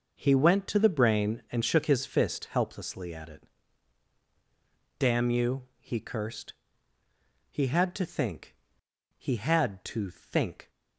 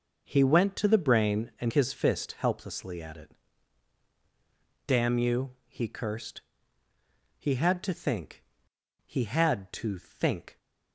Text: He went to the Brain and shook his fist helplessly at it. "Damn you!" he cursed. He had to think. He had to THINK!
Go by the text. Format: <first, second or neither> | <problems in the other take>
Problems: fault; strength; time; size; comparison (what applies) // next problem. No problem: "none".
first | skips "shook"; at 1.7 s